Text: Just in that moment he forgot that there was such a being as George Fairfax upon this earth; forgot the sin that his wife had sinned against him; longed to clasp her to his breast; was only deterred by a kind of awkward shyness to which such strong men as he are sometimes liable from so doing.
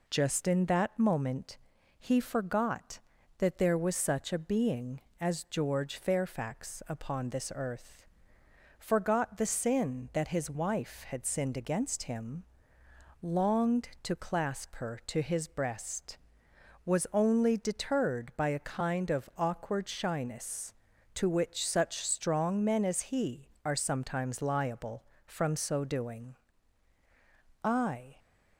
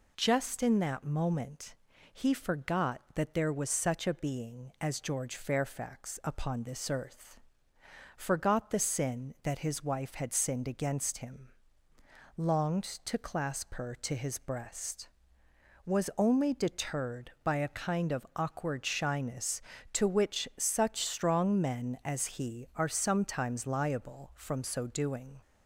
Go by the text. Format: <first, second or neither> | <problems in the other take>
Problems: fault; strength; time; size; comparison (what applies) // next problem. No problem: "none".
second | pauses between "moment" and "he"; at 1.5 s; 0.42 s long; also in the second // goes on to say "I"; from 27.6 s on; 0.54 s long